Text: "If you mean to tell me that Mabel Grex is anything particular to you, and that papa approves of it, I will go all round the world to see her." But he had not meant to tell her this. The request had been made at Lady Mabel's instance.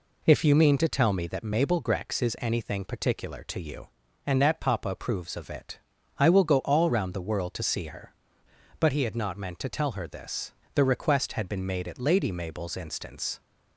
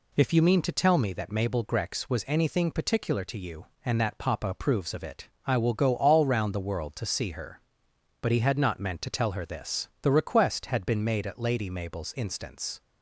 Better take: first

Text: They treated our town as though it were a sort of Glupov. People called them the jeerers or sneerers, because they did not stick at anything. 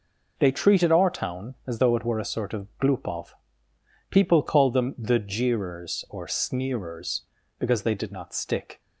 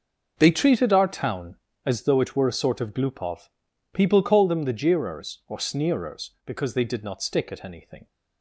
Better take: second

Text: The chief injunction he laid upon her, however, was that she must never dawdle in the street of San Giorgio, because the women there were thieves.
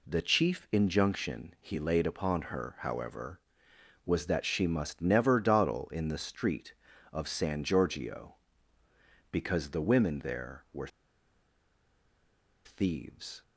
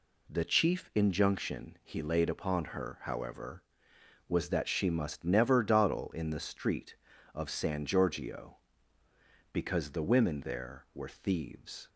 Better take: second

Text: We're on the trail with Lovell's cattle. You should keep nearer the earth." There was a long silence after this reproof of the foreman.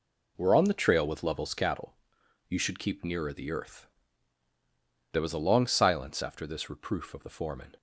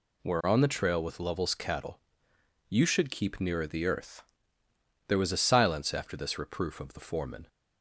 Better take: first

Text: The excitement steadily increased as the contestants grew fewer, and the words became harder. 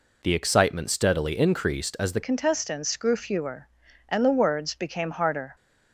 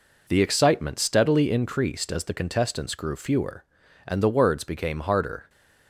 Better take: second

